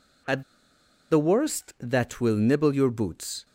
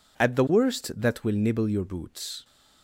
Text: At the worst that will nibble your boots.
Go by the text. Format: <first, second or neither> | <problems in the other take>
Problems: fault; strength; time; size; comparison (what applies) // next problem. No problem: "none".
second | pauses between "At" and "the"; noticeable; at 0.4 s; 0.68 s long